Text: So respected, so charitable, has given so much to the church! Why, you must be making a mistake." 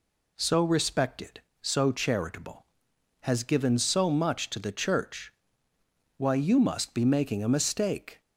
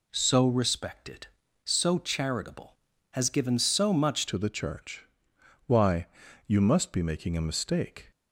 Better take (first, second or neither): first